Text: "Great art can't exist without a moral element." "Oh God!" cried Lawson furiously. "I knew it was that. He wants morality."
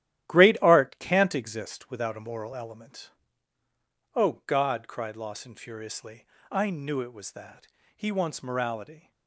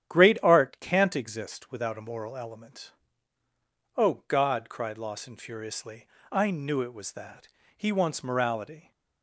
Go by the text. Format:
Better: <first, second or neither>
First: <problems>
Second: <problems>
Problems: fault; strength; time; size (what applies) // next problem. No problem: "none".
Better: second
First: gets quieter; strong; throughout; 9 dB // starts louder than the rest; strong; until 1.3 s; 12.5 dB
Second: starts louder than the rest; strong; until 1.1 s; 10 dB